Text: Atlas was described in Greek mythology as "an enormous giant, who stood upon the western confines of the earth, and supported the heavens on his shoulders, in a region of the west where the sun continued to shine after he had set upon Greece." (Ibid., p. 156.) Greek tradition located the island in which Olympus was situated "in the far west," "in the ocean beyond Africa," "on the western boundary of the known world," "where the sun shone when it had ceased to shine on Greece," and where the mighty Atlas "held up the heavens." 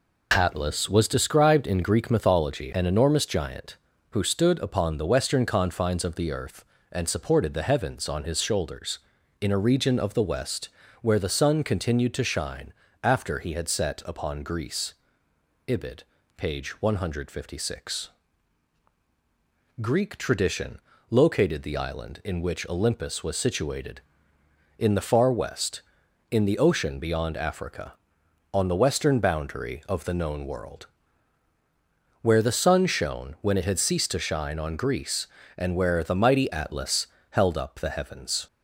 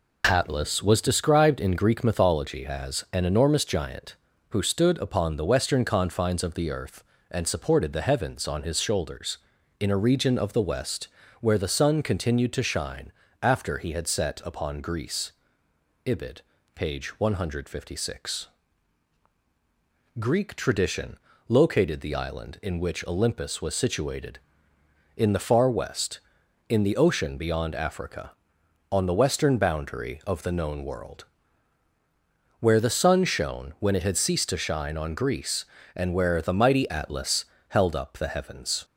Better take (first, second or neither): second